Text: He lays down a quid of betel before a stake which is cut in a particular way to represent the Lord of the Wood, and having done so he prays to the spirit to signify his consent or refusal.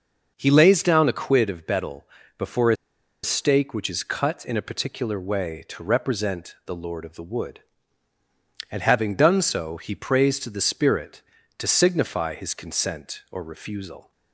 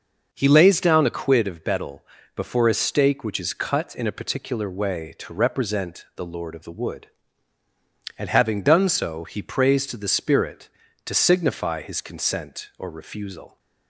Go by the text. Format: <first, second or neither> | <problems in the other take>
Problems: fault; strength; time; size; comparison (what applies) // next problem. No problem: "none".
second | pauses between "betel" and "before"; slight; at 2.0 s; 0.32 s long; slight in the second // pauses between "a" and "stake"; noticeable; at 2.7 s; 0.47 s long